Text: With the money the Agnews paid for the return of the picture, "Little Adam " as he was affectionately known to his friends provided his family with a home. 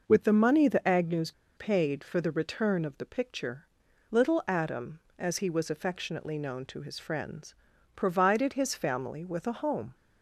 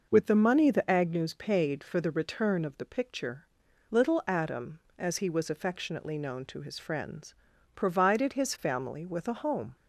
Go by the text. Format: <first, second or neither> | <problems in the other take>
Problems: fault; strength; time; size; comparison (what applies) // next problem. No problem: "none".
second | pauses between "Agnews" and "paid"; slight; at 1.3 s; 0.25 s long // pauses between "friends" and "provided"; at 7.5 s; 0.42 s long; also in the second